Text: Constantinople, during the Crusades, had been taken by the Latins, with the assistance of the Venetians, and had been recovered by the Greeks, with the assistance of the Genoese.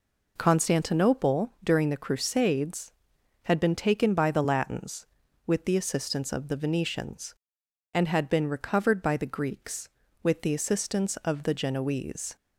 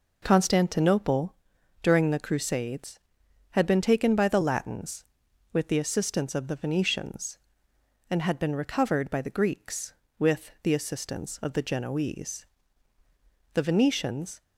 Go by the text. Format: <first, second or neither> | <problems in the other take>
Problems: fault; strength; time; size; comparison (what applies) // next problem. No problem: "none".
first | goes on to say "The Venetians"; noticeable; from 13.5 s on; 0.88 s long